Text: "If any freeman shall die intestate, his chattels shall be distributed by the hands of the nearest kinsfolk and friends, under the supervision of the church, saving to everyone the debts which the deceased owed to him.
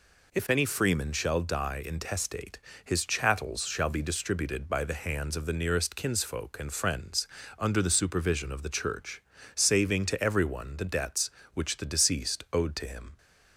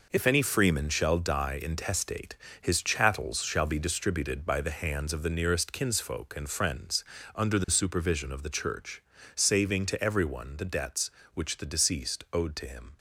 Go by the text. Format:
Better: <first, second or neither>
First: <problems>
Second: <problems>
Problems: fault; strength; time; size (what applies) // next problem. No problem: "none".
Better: first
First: none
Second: gets quieter; strong; throughout; 9.5 dB